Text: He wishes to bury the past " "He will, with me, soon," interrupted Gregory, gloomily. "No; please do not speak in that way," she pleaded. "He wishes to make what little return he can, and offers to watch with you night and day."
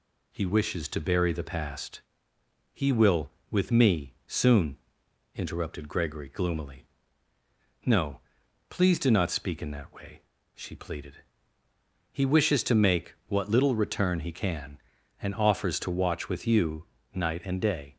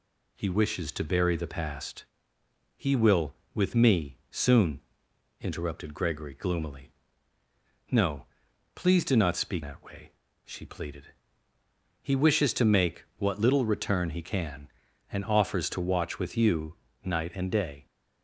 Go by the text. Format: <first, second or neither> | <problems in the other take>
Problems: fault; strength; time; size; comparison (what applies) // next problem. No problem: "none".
first | skips "in"; at 9.6 s // pauses between "you" and "night"; slight; at 16.7 s; 0.26 s long; slight in the first